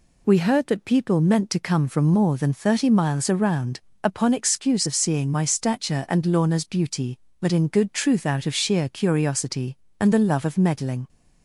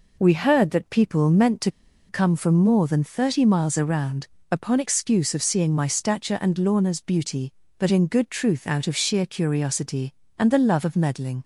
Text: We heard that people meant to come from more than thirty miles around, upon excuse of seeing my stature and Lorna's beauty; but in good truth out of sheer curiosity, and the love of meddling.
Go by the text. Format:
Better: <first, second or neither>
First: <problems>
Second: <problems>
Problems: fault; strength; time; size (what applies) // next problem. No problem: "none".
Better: first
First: none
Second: pauses between "to" and "come"; at 1.6 s; 0.38 s long